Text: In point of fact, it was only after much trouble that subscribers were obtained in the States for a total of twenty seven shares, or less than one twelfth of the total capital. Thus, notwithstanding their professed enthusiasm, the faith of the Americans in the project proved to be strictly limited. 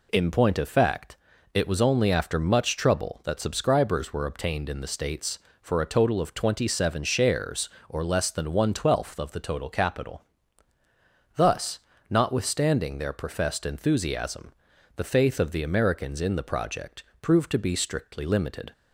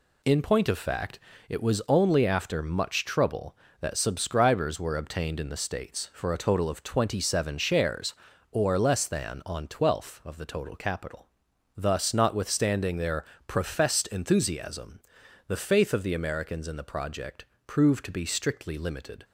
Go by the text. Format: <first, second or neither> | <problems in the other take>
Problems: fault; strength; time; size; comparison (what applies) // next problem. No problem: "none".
first | says "on" for "one"; at 9.4 s // pauses between "their" and "professed"; slight; at 13.2 s; 0.24 s long // pauses between "project" and "proved"; slight; at 17.4 s; 0.20 s long; slight in the first